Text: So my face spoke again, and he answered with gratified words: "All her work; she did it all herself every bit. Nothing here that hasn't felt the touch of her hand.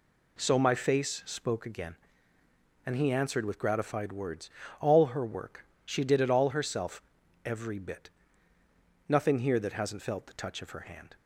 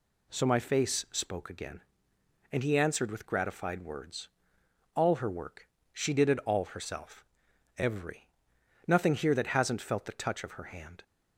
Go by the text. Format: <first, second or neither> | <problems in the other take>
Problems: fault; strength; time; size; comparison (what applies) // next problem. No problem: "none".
first | pauses between "herself" and "every"; noticeable; at 7.2 s; 0.54 s long; also in the first // skips "bit"; at 8.5 s